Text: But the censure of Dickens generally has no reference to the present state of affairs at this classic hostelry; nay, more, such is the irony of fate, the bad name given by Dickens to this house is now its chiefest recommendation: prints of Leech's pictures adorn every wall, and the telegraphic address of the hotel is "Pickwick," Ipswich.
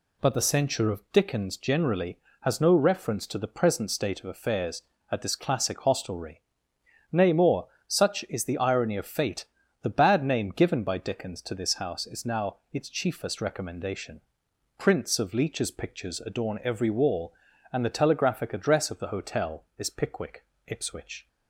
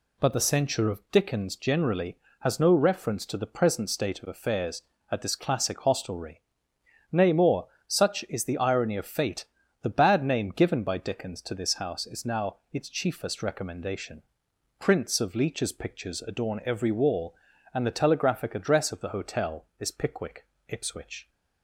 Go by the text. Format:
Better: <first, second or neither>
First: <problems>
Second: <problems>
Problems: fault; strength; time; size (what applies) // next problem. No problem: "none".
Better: neither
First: pauses between "now" and "its"; slight; at 12.5 s; 0.16 s long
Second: pauses between "now" and "its"; slight; at 12.5 s; 0.16 s long